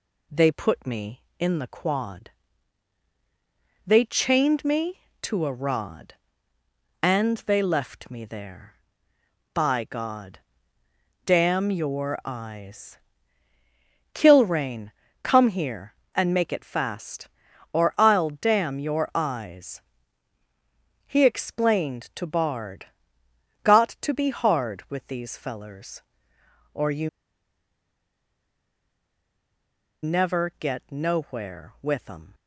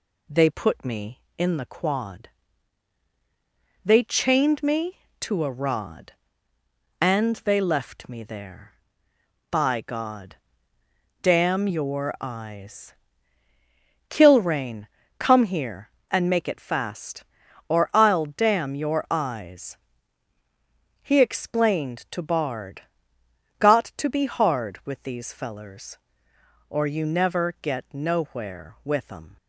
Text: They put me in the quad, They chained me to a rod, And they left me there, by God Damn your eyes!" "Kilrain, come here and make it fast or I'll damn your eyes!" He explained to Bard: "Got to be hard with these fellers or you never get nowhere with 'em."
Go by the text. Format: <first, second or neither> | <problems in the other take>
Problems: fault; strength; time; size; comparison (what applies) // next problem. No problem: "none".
second | pauses between "God" and "Damn"; noticeable; at 10.3 s; 0.88 s long; noticeable in the second // pauses between "you" and "never"; strong; at 27.0 s; 2.9 s long